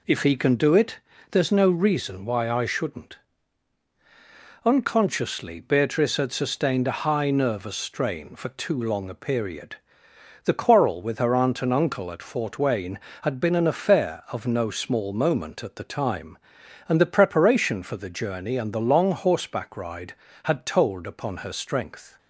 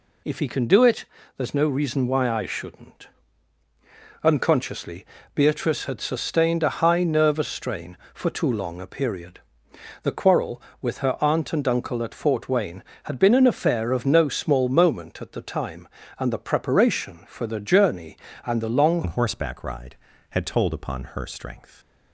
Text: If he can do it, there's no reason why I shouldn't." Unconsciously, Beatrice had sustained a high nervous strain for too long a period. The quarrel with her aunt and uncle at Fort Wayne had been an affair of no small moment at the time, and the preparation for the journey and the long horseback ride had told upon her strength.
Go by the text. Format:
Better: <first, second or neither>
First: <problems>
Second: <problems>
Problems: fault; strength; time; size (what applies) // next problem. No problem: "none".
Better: first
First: none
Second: changes voice at "horseback"; from 19.0 s on; 2.7 s long